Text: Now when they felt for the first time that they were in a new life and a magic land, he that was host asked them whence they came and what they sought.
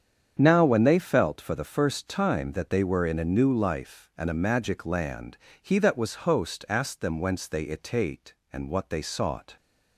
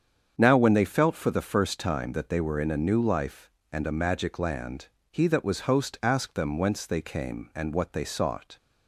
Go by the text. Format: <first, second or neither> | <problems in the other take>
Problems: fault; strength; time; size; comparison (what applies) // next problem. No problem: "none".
second | starts louder than the rest; strong; until 1.4 s; 8 dB; strong in the second // says "itate" for "came"; at 7.6 s